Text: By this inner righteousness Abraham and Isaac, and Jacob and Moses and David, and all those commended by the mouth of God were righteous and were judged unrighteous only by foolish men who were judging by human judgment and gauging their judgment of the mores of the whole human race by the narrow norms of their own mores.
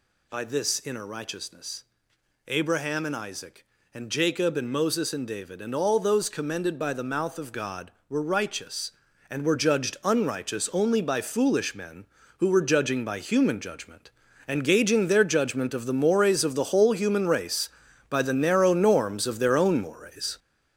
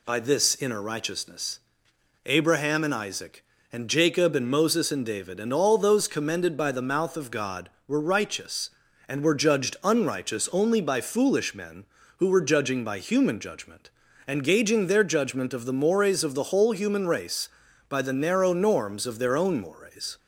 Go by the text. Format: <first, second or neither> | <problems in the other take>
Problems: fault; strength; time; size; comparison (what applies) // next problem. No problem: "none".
second | gets louder; throughout; 7 dB // pauses between "righteousness" and "Abraham"; noticeable; at 1.8 s; 0.64 s long; noticeable in the second